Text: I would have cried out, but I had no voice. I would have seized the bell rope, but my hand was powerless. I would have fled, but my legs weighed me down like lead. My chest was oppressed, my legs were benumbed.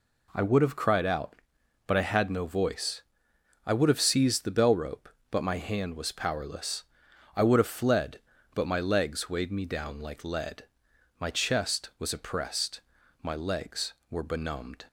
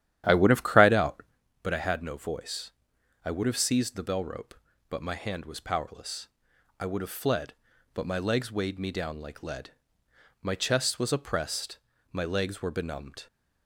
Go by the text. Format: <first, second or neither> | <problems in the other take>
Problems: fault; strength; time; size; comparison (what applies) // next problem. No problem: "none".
first | starts louder than the rest; strong; until 1.4 s; 11 dB